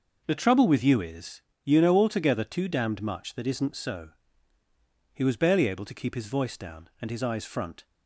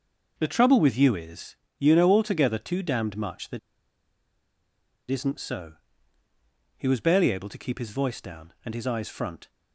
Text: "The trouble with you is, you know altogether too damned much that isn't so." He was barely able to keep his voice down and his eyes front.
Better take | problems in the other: first | pauses between "that" and "isn't"; strong; at 3.5 s; 1.5 s long

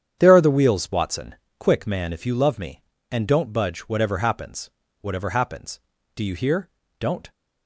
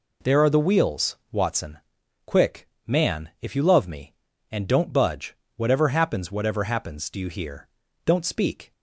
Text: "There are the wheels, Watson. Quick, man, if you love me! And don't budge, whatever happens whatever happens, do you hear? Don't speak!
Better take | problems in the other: second | starts louder than the rest; strong; until 1.2 s; 8.5 dB // pauses between "happens" and "whatever"; slight; at 4.6 s; 0.32 s long // stops before "speak"; at 7.3 s

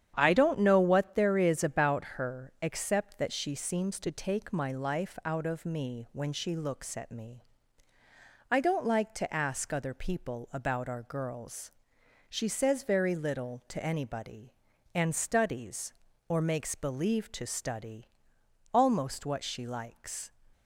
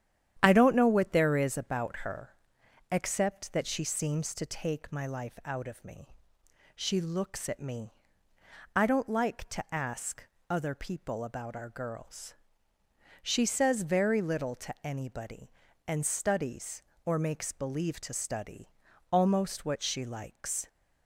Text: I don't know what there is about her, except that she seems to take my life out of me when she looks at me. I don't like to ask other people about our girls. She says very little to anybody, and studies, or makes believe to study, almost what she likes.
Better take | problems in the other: first | starts louder than the rest; strong; until 1.4 s; 10 dB; strong in the first // skips "when"; at 6.4 s // pauses between "ask" and "other"; slight; at 10.2 s; 0.24 s long

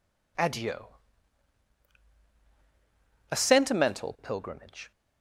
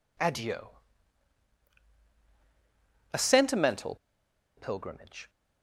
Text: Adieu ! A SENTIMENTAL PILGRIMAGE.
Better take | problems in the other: first | pauses between "SENTIMENTAL" and "PILGRIMAGE"; noticeable; at 3.9 s; 0.60 s long

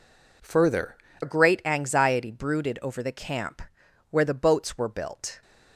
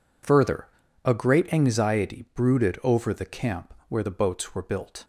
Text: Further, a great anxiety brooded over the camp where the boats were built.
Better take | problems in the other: second | changes voice at "a"; from 1.2 s on; 4.2 s long // pauses between "camp" and "where"; noticeable; at 3.6 s; 0.48 s long; slight in the second

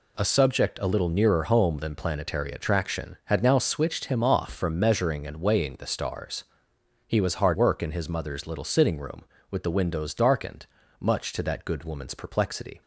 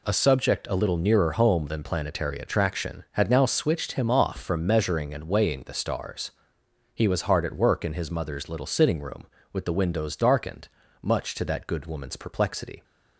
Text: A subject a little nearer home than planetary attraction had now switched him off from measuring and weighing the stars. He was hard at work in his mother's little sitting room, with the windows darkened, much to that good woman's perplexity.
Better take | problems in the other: second | skips "at"; at 7.5 s

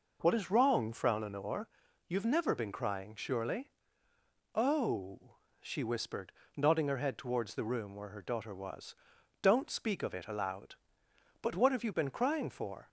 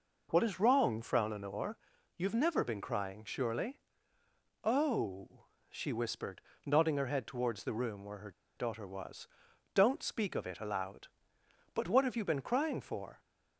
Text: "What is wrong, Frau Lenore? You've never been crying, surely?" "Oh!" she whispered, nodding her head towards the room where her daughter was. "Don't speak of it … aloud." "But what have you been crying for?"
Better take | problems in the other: first | pauses between "her" and "daughter"; slight; at 8.2 s; 0.26 s long

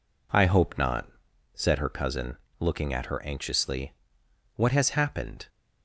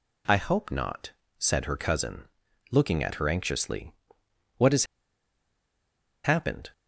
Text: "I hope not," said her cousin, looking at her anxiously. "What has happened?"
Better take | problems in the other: first | pauses between "has" and "happened"; strong; at 4.8 s; 1.3 s long

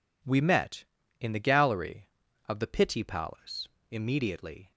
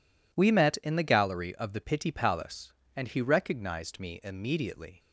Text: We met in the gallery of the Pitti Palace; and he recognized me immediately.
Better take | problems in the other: second | skips "and he recognized me"; at 3.7 s

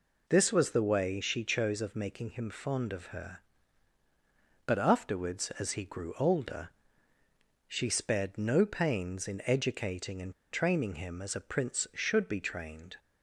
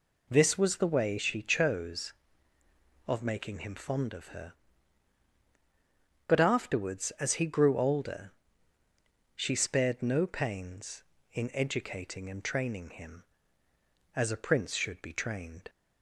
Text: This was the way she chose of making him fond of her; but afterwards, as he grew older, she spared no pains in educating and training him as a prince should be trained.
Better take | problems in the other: second | pauses between "and" and "training"; slight; at 10.3 s; 0.18 s long

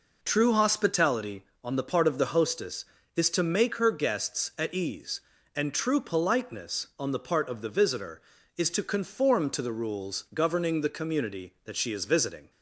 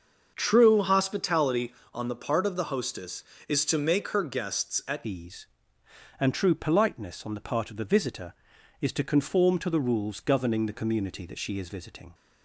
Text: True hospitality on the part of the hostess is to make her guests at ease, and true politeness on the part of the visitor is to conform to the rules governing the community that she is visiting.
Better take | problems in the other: first | starts louder than the rest; until 1.3 s; 6.5 dB // changes voice at "ease"; from 5.0 s on; 7.1 s long

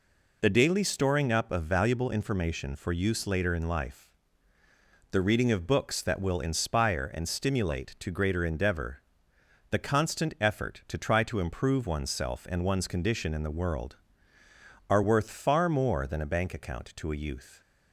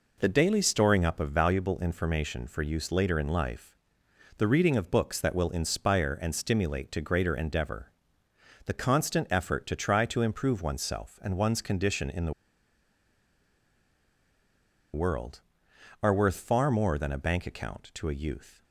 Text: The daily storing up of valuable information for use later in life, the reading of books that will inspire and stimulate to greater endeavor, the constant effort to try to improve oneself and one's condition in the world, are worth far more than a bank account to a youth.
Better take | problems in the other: first | pauses between "the" and "world"; strong; at 12.3 s; 2.6 s long

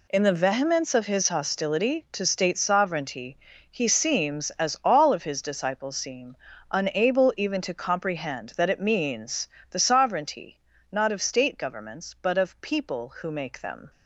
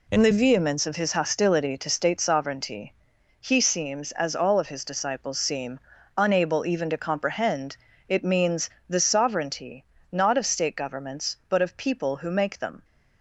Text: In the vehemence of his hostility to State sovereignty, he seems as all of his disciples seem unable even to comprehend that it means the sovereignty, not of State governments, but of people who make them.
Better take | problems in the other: first | pauses between "seem" and "unable"; slight; at 5.8 s; 0.36 s long; also in the first // skips "that"; at 7.9 s // pauses between "means" and "the"; slight; at 8.7 s; 0.18 s long; slight in the first

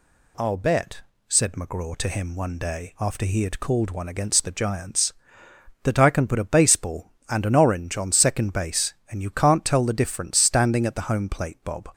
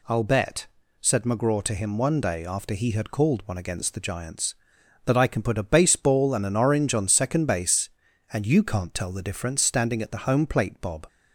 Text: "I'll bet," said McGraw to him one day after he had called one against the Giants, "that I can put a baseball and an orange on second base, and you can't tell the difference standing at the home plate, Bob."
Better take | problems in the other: neither | none

